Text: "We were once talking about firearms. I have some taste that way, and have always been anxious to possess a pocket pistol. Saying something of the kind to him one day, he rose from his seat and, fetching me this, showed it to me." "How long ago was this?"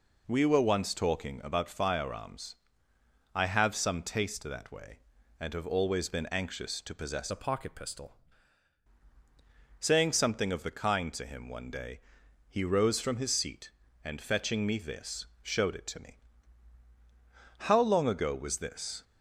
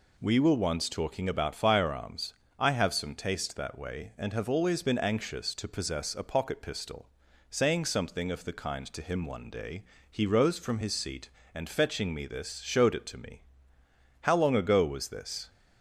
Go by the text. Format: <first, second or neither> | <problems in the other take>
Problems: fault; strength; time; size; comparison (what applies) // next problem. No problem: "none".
second | changes voice from "a" to "pistol"; from 7.3 to 8.1 s; 0.8 s long